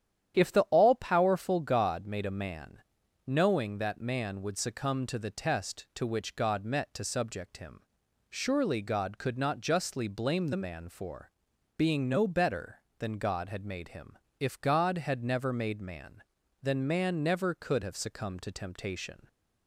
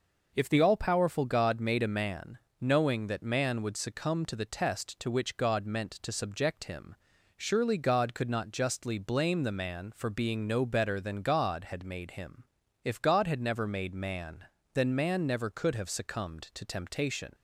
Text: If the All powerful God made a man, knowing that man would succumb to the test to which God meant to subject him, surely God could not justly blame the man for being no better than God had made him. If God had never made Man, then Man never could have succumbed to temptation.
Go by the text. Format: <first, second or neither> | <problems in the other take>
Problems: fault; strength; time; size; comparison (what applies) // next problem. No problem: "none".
second | starts louder than the rest; strong; until 1.4 s; 10 dB // says "met" for "meant"; at 6.6 s // pauses between "for" and "being"; noticeable; at 11.3 s; 0.46 s long